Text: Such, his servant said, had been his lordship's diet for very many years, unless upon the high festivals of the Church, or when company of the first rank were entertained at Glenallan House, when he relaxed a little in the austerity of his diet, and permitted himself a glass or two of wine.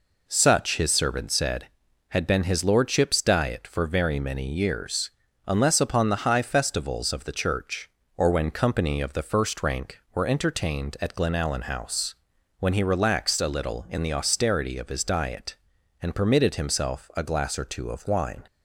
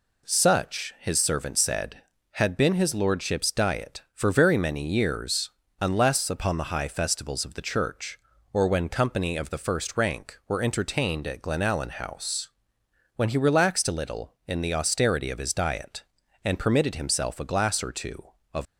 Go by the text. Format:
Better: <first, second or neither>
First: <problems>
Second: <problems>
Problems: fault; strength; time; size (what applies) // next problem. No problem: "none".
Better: first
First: none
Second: stops before "wine"; at 18.6 s